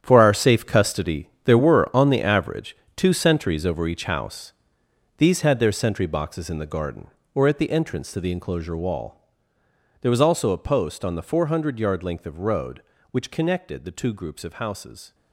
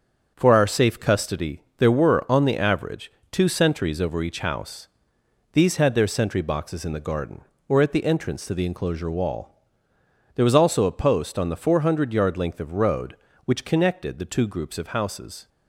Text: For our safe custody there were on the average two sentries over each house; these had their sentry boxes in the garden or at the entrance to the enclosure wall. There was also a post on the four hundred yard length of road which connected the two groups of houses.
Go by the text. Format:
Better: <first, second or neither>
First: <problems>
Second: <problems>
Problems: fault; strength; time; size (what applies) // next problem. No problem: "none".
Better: second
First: gets quieter; strong; throughout; 13 dB // starts louder than the rest; strong; until 1.0 s; 9 dB // pauses between "custody" and "there"; slight; at 1.2 s; 0.16 s long // pauses between "average" and "two"; slight; at 2.7 s; 0.20 s long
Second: starts louder than the rest; until 1.3 s; 7 dB // pauses between "custody" and "there"; slight; at 1.6 s; 0.16 s long // pauses between "average" and "two"; slight; at 3.1 s; 0.20 s long